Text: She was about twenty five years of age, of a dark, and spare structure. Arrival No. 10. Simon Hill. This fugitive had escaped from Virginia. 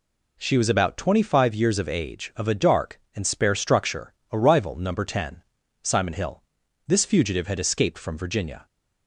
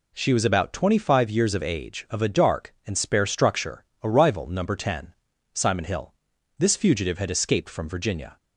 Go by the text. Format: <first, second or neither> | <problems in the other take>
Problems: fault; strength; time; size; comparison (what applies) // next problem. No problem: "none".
neither | none